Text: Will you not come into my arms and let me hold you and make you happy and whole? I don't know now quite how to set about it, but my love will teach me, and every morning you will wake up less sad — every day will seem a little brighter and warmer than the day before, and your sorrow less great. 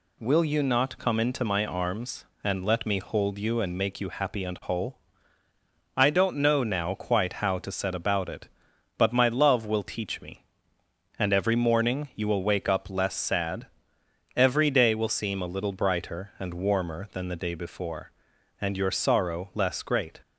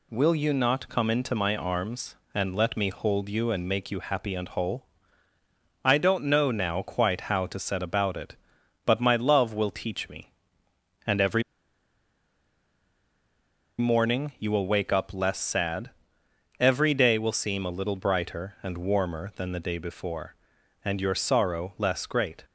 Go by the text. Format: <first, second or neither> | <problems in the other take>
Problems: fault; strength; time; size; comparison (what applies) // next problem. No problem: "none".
first | pauses between "every" and "morning"; strong; at 11.4 s; 2.3 s long